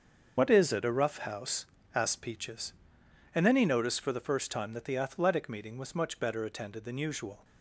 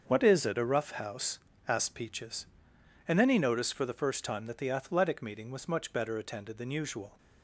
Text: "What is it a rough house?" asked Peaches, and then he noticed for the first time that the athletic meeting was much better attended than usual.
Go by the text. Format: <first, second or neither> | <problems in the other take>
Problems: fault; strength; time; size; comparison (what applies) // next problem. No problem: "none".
second | loses the start of "What"; at 0.3 s; 35 ms // starts louder than the rest; until 1.3 s; 6.5 dB; also in the second